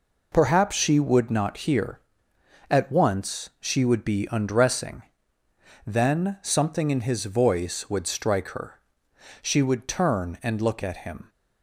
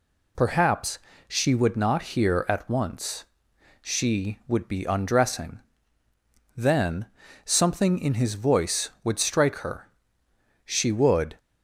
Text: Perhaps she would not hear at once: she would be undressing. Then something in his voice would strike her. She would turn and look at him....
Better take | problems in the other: first | pauses between "Perhaps" and "she"; slight; at 0.9 s; 0.30 s long // pauses between "Then" and "something"; at 7.0 s; 0.40 s long // stops before "turn and look at him"; at 11.3 s

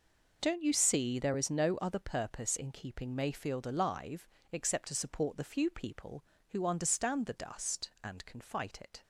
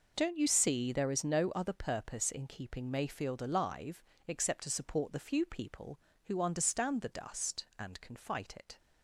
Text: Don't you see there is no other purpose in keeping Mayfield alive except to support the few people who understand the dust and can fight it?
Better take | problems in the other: neither | pauses between "alive" and "except"; slight; the same in both

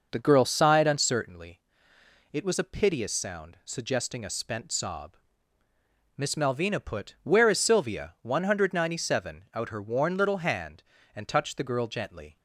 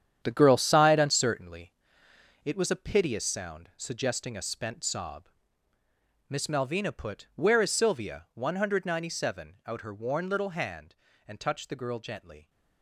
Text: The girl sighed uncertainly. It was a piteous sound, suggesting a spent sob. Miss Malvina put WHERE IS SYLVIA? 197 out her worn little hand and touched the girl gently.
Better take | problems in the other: first | gets quieter; strong; throughout; 10 dB

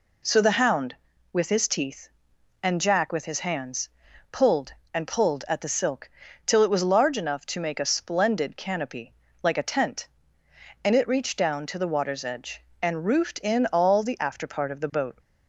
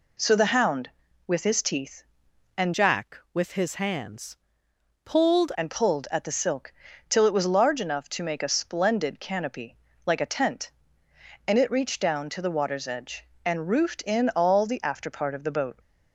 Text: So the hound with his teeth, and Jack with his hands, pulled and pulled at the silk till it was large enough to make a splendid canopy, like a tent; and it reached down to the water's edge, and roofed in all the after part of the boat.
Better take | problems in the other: first | changes voice from "Jack" to "pulled"; from 2.7 to 5.5 s; 2.8 s long // pauses between "silk" and "till"; slight; at 6.7 s; 0.36 s long; slight in the first

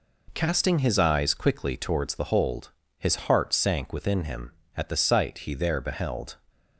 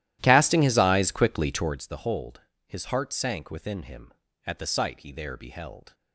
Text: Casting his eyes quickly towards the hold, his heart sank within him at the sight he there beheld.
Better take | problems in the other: first | starts louder than the rest; strong; until 1.8 s; 13.5 dB

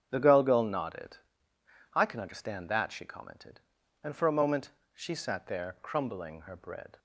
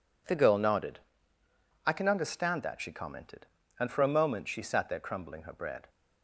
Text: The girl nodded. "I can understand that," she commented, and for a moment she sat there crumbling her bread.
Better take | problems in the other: second | starts louder than the rest; strong; until 1.1 s; 9 dB // says "girl" twice; at 0.4 s // pauses between "moment" and "she"; slight; at 4.7 s; 0.22 s long

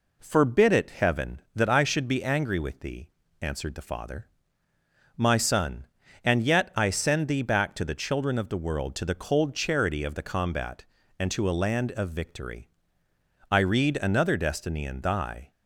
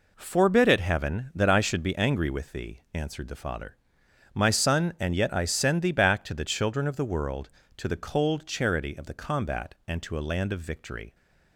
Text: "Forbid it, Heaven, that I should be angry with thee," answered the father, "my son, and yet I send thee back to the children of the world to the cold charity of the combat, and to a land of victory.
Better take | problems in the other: second | goes on to say "I read another destiny in thy"; strong; from 13.4 s on; 2.0 s long

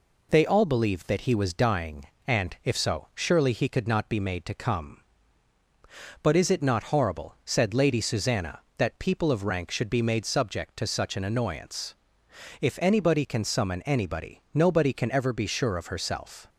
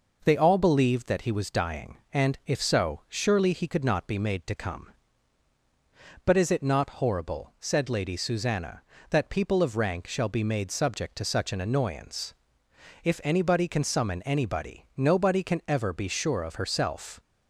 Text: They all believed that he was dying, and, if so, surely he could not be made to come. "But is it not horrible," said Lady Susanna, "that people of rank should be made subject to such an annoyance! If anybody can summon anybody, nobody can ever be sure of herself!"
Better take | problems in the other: first | says "shall" for "should"; at 10.0 s

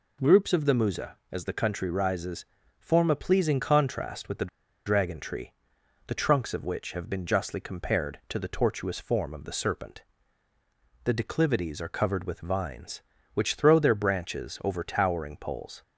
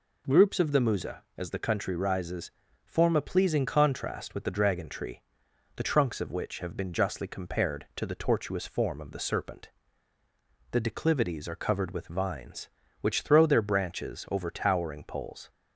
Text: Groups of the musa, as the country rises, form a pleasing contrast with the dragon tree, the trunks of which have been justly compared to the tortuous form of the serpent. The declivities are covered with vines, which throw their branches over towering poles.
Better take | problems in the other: second | pauses between "the" and "dragon"; at 4.4 s; 0.38 s long

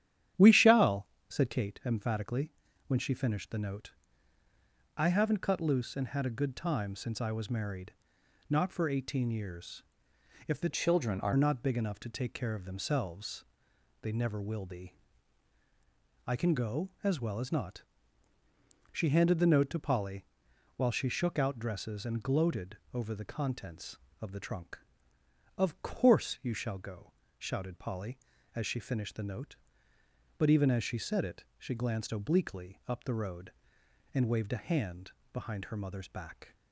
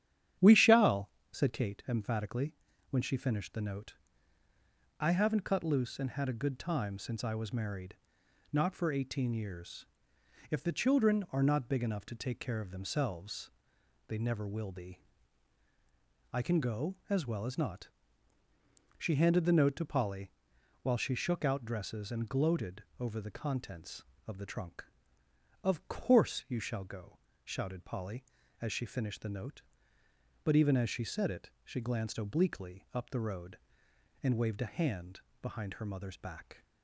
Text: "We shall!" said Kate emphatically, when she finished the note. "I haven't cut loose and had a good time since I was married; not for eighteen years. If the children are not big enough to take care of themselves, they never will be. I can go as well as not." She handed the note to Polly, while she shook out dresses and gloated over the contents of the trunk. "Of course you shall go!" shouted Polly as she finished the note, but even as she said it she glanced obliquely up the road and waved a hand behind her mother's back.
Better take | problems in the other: second | starts louder than the rest; strong; until 1.5 s; 10.5 dB; strong in the second // changes voice from "children" to "are"; from 10.7 to 11.3 s; 0.6 s long // pauses between "gloated" and "over"; slight; at 22.7 s; 0.16 s long; slight in the second // pauses between "hand" and "behind"; slight; at 35.1 s; 0.22 s long; slight in the second

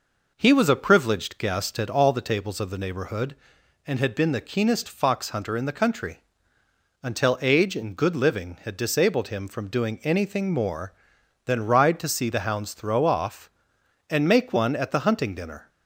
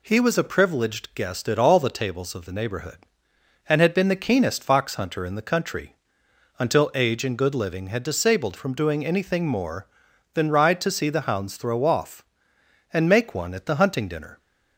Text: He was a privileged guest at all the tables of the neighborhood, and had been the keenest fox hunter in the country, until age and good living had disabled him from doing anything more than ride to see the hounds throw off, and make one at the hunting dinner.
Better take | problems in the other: first | skips "him"; at 8.5 s

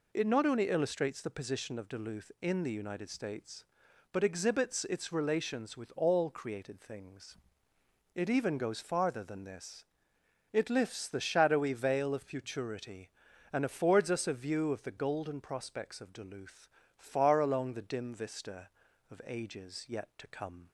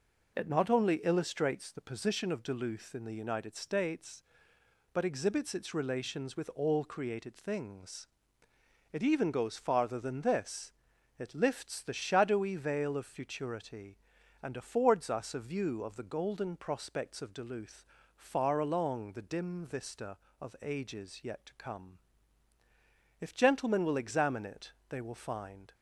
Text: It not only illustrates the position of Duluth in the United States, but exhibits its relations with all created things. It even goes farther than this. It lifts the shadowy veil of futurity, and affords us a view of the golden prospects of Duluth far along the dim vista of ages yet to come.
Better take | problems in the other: first | pauses between "Duluth" and "far"; slight; at 17.8 s; 0.32 s long; slight in the first // goes on to say "If gentlemen will examine it they will find"; strong; from 23.1 s on; 2.5 s long

